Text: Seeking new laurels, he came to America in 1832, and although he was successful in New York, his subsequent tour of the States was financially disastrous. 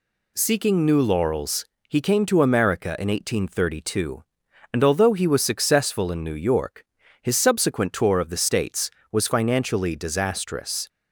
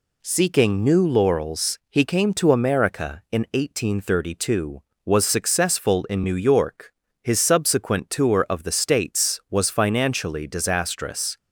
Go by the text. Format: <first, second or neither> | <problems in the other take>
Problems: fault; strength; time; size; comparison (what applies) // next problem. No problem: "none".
first | skips "and although he"; at 4.9 s